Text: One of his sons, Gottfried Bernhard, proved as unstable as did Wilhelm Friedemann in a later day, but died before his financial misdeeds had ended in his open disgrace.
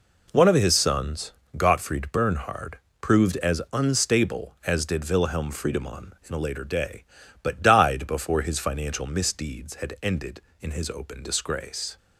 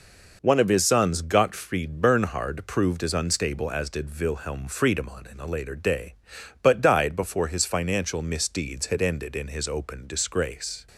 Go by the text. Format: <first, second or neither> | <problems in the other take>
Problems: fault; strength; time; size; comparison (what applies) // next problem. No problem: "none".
neither | none